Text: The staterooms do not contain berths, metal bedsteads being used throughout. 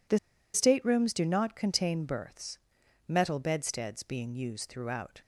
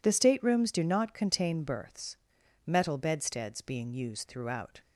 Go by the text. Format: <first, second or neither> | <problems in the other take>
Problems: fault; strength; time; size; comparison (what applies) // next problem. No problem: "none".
second | pauses between "The" and "staterooms"; at 0.1 s; 0.36 s long